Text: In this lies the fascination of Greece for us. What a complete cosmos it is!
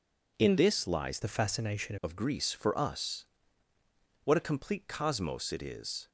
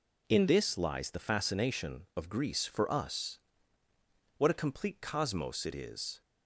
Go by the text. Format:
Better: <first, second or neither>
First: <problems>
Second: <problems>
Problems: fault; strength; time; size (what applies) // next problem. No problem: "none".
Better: second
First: changes voice from "the" to "fascination"; from 1.2 to 1.9 s; 0.7 s long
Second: none